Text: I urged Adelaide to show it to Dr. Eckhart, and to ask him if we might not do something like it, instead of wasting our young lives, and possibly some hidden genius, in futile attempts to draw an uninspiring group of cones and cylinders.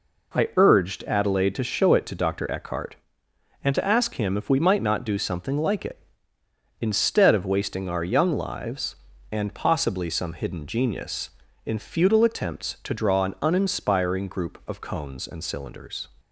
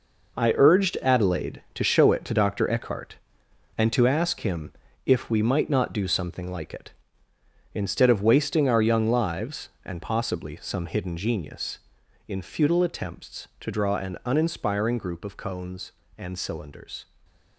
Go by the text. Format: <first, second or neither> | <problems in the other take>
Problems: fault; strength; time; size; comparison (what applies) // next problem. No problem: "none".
first | gets quieter; strong; throughout; 9.5 dB // pauses between "him" and "if"; slight; at 4.7 s; 0.32 s long // stays silent after the last word; slight; from 17.0 s on; 0.5 s long